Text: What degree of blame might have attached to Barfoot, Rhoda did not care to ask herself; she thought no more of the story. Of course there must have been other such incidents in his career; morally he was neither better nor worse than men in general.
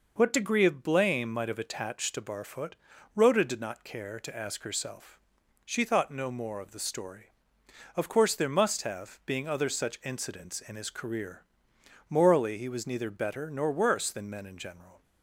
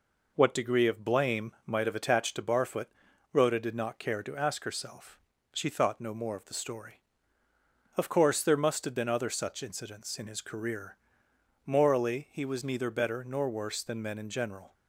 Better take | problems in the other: second | says "being" for "been"; at 9.2 s

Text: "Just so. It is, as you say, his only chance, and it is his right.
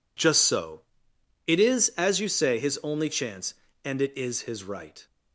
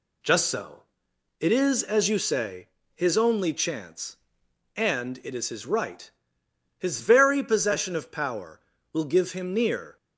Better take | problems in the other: first | goes on to say "His very possession of power will give him near"; strong; from 6.7 s on; 3.1 s long

